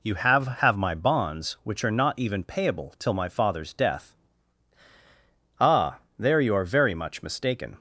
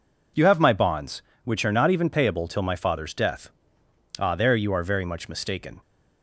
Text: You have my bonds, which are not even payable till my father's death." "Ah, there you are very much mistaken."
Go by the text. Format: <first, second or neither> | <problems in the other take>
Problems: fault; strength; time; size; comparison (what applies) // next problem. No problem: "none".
second | says "have" twice; at 0.4 s